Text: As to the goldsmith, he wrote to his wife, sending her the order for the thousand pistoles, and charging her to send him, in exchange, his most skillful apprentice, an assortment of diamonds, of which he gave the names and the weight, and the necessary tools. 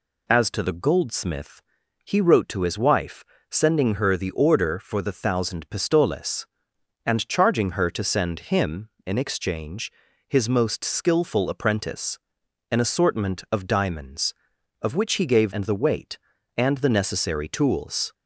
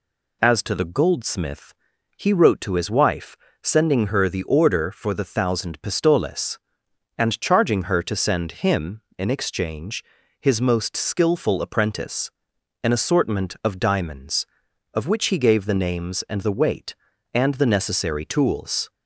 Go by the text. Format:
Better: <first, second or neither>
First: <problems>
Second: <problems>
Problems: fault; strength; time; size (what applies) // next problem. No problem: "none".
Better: second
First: skips "the names"; at 15.5 s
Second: none